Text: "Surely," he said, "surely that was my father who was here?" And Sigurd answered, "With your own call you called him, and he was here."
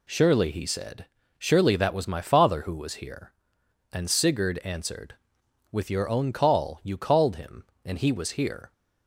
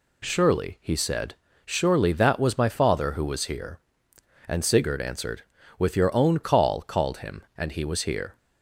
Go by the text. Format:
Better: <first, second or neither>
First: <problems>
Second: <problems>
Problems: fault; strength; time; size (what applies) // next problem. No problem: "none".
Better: first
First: none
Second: skips "you"; at 6.8 s